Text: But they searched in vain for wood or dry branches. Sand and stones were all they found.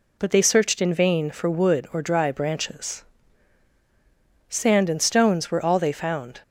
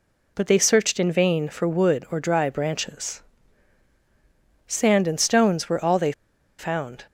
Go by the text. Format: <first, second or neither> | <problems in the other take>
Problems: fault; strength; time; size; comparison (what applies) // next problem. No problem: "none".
first | pauses between "they" and "found"; noticeable; at 6.1 s; 0.46 s long